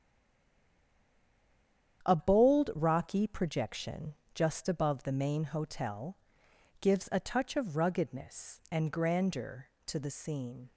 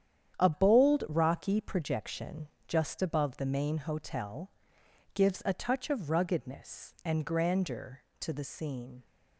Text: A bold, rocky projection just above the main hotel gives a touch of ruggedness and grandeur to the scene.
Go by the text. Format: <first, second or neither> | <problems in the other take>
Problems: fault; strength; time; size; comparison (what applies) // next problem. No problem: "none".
second | stays silent before the first word; noticeable; until 2.0 s; 2.0 s long // starts louder than the rest; strong; until 3.0 s; 9 dB; strong in the second // pauses between "projection" and "just"; slight; at 4.1 s; 0.18 s long; slight in the second // pauses between "hotel" and "gives"; noticeable; at 6.1 s; 0.62 s long; noticeable in the second